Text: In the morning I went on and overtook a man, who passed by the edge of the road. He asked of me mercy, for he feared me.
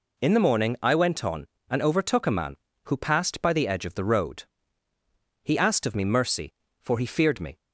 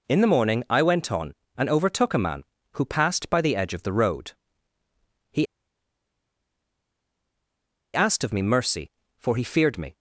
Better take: first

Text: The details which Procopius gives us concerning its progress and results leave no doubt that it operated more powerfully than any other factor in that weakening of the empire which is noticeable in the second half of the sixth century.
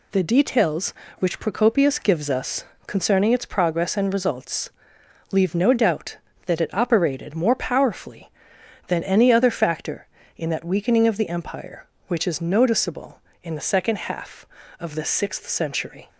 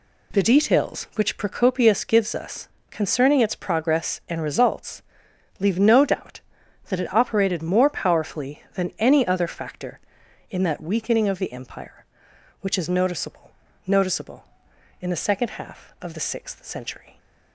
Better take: first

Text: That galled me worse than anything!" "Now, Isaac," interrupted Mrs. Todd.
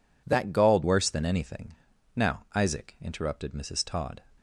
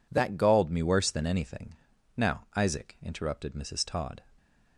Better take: second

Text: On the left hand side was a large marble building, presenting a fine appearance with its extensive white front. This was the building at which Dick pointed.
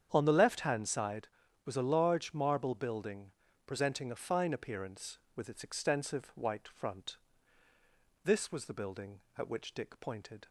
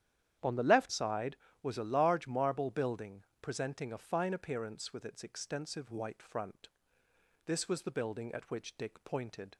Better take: first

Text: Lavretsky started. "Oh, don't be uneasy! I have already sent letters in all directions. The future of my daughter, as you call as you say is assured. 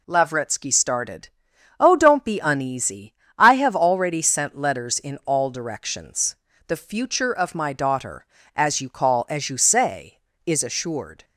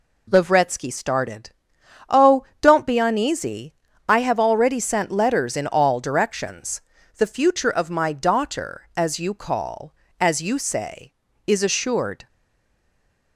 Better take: first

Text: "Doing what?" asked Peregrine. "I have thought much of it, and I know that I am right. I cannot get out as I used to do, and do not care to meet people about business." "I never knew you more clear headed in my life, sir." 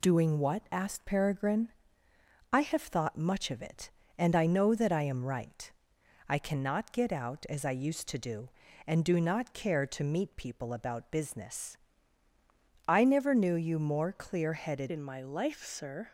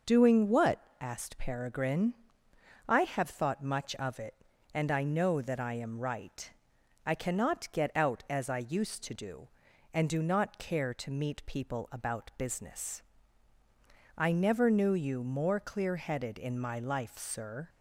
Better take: second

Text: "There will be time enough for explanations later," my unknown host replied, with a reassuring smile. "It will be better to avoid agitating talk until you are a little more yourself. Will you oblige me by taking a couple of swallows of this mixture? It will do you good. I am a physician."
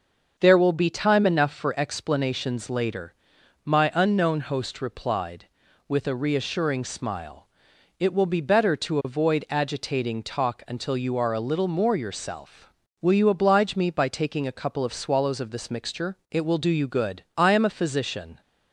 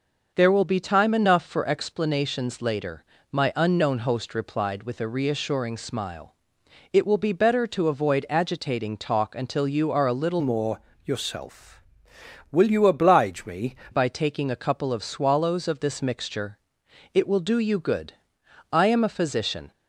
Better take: first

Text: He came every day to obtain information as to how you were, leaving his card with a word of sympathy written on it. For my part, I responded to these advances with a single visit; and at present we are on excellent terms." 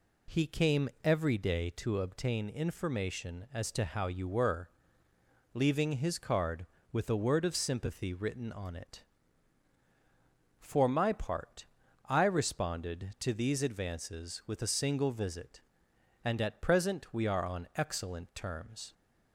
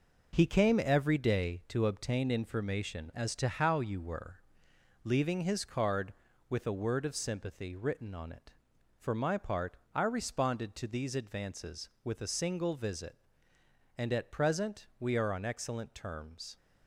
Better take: first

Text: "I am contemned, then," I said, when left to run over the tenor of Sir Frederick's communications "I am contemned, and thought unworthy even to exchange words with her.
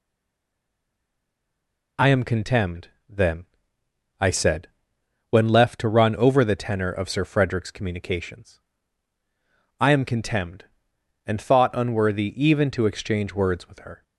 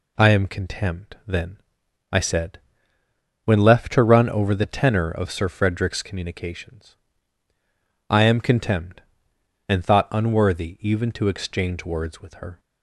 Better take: second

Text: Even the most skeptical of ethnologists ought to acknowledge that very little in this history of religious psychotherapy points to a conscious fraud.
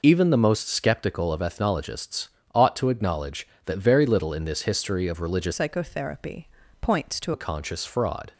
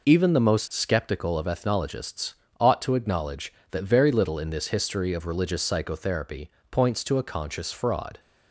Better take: second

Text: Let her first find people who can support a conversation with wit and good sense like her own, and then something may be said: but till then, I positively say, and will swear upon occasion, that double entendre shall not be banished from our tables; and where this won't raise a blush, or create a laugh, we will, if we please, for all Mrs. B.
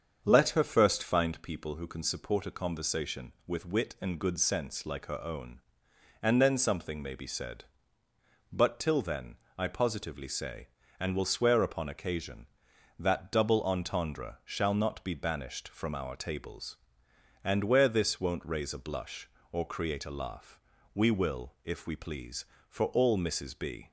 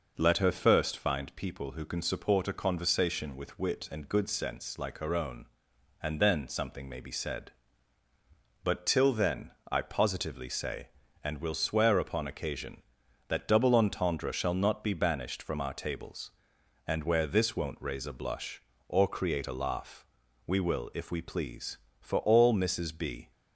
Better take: second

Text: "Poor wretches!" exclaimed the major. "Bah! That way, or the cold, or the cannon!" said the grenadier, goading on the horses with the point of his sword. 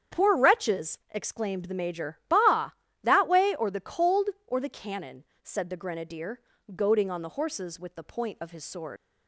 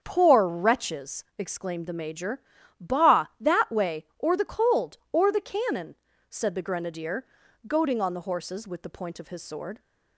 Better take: second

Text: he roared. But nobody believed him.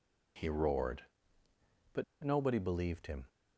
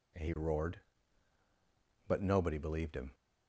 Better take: second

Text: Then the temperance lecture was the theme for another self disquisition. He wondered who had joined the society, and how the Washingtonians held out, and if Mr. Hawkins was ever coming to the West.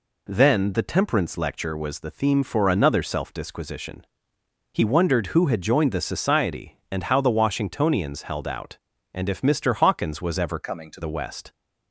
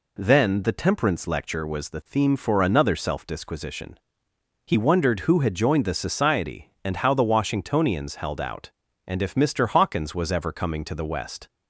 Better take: second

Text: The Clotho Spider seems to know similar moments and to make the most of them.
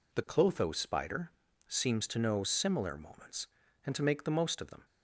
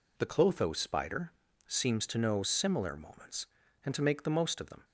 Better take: neither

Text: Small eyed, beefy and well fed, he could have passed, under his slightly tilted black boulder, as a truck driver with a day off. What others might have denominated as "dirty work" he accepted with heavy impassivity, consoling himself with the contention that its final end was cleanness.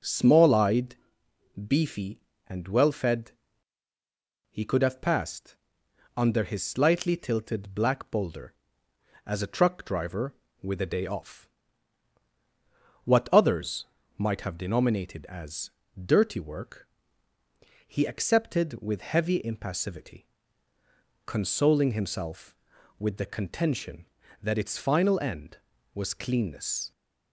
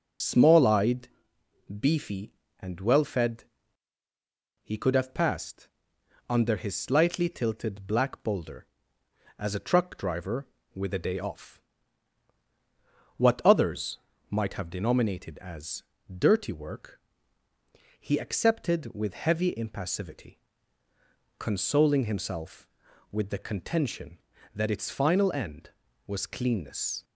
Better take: first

